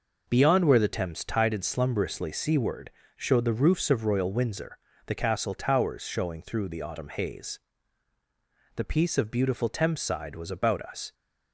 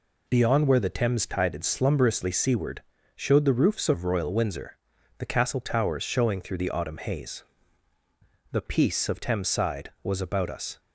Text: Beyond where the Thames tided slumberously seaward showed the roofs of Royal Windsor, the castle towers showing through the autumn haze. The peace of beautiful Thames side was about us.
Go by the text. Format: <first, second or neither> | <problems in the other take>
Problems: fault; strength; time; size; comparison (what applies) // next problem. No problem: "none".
first | pauses between "seaward" and "showed"; slight; at 2.8 s; 0.32 s long; slight in the first // skips "beautiful"; at 9.2 s